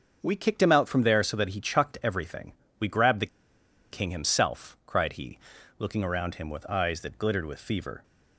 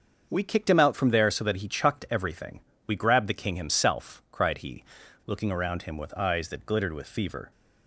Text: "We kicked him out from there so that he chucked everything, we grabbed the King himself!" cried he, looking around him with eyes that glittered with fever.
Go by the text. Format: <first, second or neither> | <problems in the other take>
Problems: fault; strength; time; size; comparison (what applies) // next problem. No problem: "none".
second | starts louder than the rest; until 1.2 s; 6.5 dB; also in the second // pauses between "the" and "King"; noticeable; at 3.2 s; 0.64 s long